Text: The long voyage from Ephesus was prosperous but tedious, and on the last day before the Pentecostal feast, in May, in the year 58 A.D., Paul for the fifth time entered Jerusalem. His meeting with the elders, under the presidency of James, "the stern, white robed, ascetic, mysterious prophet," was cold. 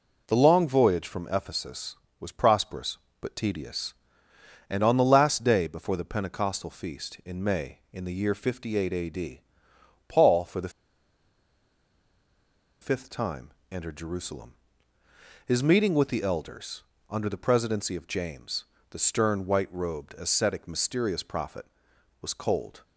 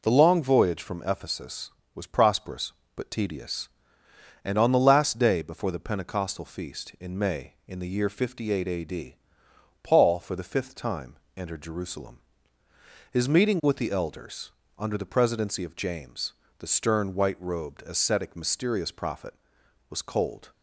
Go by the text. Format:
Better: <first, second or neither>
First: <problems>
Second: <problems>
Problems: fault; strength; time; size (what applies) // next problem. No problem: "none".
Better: second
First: pauses between "the" and "fifth"; strong; at 10.6 s; 2.1 s long // pauses between "time" and "entered"; slight; at 13.5 s; 0.20 s long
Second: pauses between "time" and "entered"; slight; at 11.1 s; 0.20 s long